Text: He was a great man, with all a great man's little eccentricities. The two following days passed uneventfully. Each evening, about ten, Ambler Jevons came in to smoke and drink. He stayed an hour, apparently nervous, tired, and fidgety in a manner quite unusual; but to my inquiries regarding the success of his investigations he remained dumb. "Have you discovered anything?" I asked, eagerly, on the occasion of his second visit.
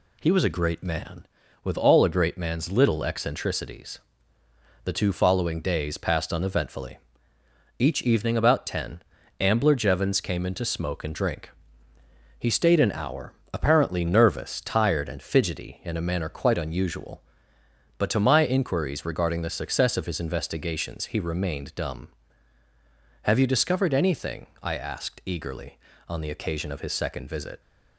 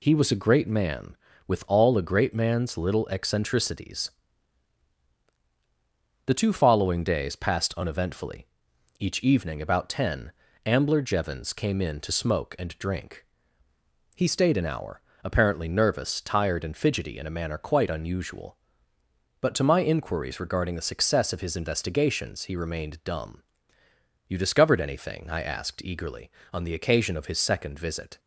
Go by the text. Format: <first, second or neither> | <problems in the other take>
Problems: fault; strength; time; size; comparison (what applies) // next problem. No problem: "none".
first | skips "Have"; at 23.8 s